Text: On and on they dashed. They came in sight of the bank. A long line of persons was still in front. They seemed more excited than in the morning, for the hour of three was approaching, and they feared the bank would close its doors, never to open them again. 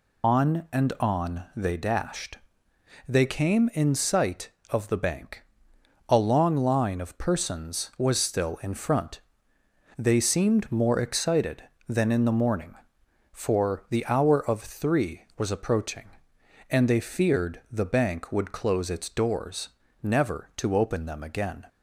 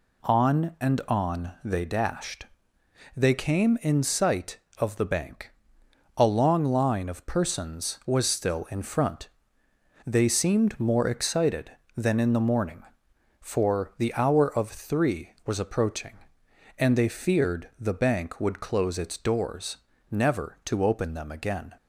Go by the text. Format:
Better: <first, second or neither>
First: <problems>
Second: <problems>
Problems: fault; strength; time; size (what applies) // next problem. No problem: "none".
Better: second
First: loses the start of "On"; at 0.2 s; 100 ms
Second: none